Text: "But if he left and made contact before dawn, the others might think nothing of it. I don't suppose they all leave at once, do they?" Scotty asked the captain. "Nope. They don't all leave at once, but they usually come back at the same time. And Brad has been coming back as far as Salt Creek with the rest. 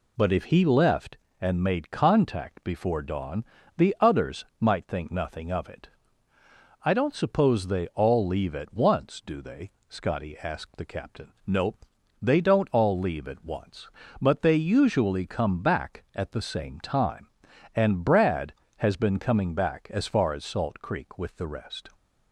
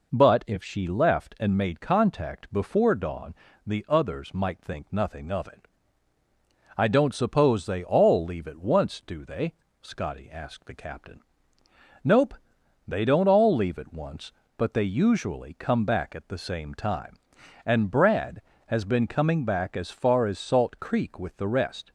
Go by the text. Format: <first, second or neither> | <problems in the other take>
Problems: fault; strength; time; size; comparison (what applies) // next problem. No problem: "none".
first | says "she" for "he"; at 0.6 s